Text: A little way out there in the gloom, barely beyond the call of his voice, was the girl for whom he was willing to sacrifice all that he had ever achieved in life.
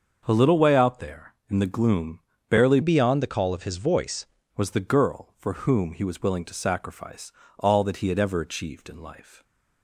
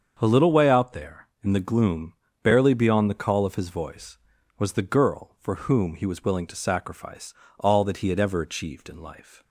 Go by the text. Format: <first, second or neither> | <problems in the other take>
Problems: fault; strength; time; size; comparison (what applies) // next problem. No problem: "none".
second | starts louder than the rest; until 1.2 s; 6.5 dB; also in the second // changes voice from "beyond" to "voice"; from 2.8 to 4.2 s; 1.4 s long // pauses between "sacrifice" and "all"; slight; at 7.3 s; 0.26 s long; slight in the second